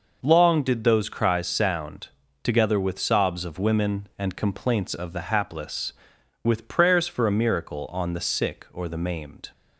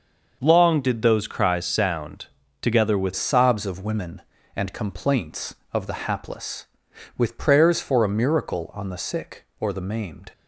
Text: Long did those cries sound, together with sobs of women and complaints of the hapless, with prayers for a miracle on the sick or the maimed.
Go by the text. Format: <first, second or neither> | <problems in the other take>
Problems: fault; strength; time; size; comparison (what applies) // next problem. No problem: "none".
first | changes voice at "sobs"; from 3.1 s on; 7.2 s long